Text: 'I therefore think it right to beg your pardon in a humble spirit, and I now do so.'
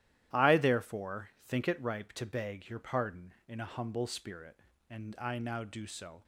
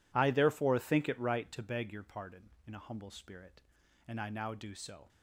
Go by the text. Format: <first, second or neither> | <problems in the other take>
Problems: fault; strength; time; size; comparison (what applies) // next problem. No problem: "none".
second | starts louder than the rest; strong; until 1.4 s; 12.5 dB // says "ripe" for "right"; at 1.8 s